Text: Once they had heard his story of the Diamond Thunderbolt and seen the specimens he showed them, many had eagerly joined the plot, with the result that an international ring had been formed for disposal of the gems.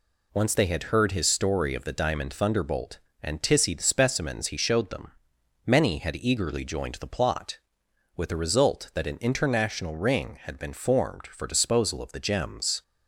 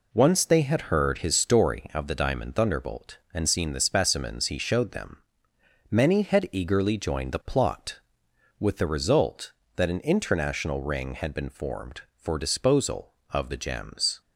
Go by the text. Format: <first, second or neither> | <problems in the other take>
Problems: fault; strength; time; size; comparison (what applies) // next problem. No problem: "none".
second | says "tissy" for "seen"; at 3.4 s